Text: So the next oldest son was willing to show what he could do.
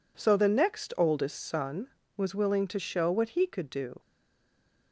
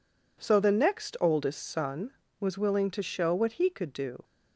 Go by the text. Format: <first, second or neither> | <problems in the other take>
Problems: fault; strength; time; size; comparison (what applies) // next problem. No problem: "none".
second | stays silent after the last word; slight; from 3.9 s on; 1.0 s long